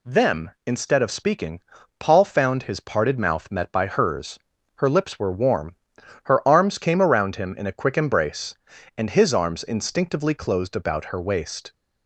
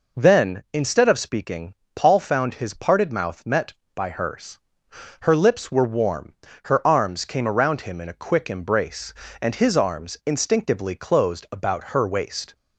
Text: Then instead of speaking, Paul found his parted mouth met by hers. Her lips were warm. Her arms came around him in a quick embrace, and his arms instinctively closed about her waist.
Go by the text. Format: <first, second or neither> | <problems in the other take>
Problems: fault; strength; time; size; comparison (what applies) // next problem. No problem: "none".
second | says "Them" for "Then"; at 0.0 s